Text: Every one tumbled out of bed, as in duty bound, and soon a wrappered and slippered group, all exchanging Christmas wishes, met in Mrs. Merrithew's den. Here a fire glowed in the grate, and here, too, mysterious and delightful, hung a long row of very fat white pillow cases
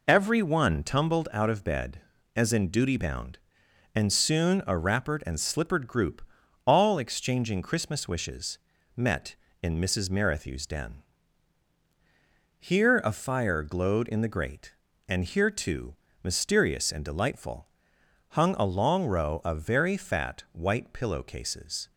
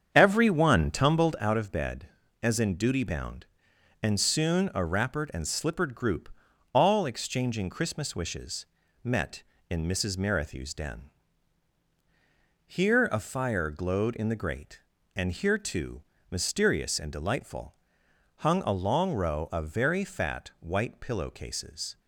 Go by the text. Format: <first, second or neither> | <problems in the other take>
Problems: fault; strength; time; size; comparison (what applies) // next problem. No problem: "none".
first | starts louder than the rest; strong; until 1.6 s; 7.5 dB